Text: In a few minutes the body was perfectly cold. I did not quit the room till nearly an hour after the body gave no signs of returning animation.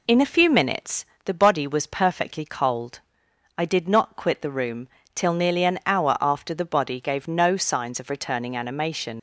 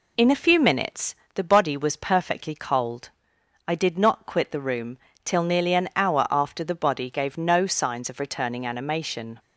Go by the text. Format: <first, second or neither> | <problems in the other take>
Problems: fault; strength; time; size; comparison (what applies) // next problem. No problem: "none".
second | pauses between "minutes" and "the"; slight; at 1.0 s; 0.20 s long; slight in the second // pauses between "room" and "till"; slight; at 4.8 s; 0.28 s long; slight in the second // leaves "animation" unfinished; at 9.1 s; 100 ms